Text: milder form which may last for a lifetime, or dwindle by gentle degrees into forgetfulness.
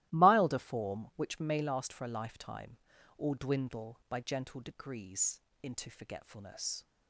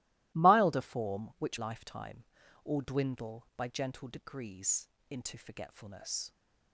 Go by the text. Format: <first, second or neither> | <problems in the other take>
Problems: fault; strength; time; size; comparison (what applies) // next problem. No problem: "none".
first | starts louder than the rest; strong; until 1.4 s; 18 dB; strong in the first // skips "may last for a"; at 1.5 s // pauses between "degrees" and "into"; slight; at 4.8 s; 0.20 s long; slight in the first